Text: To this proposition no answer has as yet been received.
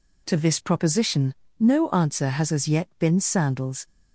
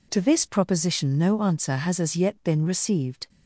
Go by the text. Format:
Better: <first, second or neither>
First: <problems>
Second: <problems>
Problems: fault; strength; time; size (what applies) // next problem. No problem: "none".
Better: second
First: pauses between "proposition" and "no"; slight; at 1.3 s; 0.26 s long // says "sandals" for "received"; at 3.1 s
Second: none